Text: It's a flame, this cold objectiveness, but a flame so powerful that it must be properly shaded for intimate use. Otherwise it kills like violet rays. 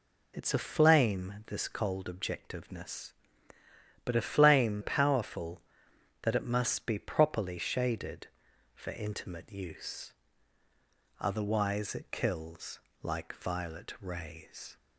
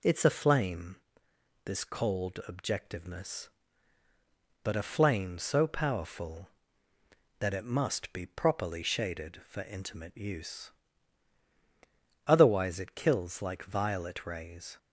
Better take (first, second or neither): second